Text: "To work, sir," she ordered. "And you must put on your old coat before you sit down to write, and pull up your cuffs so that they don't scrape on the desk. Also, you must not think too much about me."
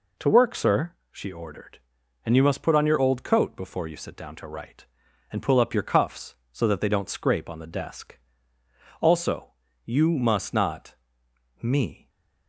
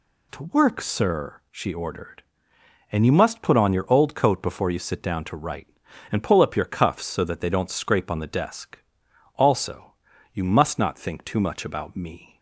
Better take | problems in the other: second | skips "think too much about"; at 11.2 s // stays silent after the last word; slight; from 11.9 s on; 0.5 s long

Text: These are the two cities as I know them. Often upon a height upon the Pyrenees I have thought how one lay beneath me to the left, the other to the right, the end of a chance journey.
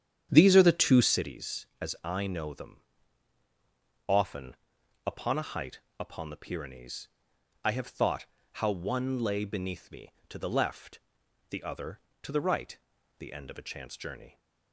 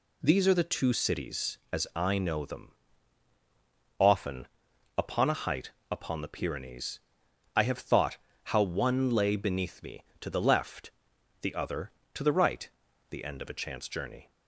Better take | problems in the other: second | starts louder than the rest; strong; until 1.2 s; 9 dB // pauses between "Often" and "upon"; noticeable; at 4.5 s; 0.48 s long; noticeable in the second // pauses between "height" and "upon"; slight; at 5.7 s; 0.18 s long; slight in the second // pauses between "Pyrenees" and "I"; noticeable; at 7.0 s; 0.56 s long; noticeable in the second // pauses between "thought" and "how"; slight; at 8.2 s; 0.28 s long; slight in the second

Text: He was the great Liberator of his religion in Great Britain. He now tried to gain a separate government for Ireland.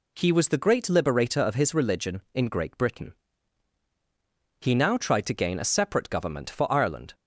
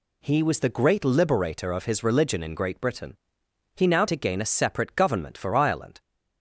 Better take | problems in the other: first | skips "tried"; at 4.0 s

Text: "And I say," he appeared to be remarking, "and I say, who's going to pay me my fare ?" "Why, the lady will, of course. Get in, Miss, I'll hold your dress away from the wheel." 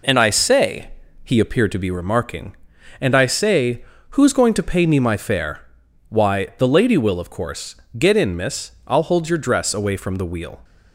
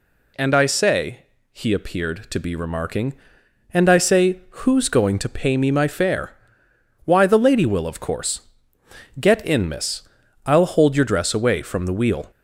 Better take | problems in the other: neither | none

